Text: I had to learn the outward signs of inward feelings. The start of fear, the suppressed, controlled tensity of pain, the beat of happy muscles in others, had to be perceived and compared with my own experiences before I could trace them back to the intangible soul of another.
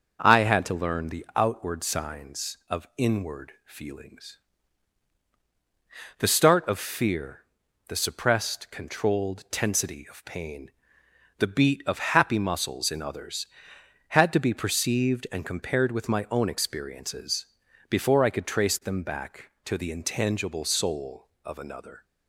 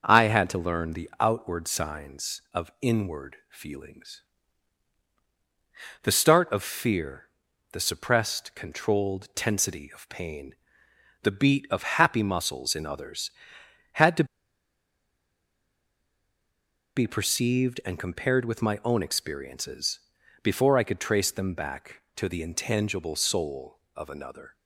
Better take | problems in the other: first | starts louder than the rest; noticeable; until 1.0 s; 6 dB // pauses between "to" and "be"; strong; at 14.2 s; 2.7 s long // pauses between "experiences" and "before"; at 19.9 s; 0.42 s long; also in the first

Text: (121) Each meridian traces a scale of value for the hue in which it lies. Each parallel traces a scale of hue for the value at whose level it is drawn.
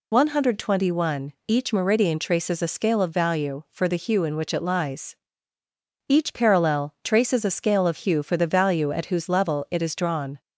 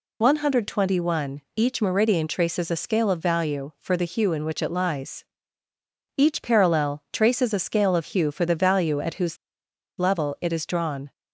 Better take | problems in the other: first | pauses between "whose" and "level"; noticeable; at 9.3 s; 0.61 s long

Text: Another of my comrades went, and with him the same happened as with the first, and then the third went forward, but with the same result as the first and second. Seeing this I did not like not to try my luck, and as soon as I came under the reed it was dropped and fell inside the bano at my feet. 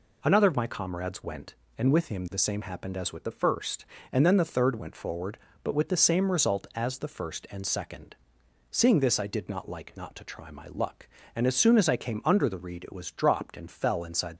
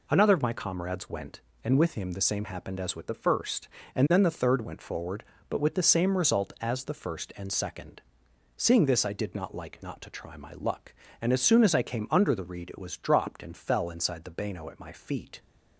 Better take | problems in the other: second | stops before "the bano at my feet"; at 14.3 s

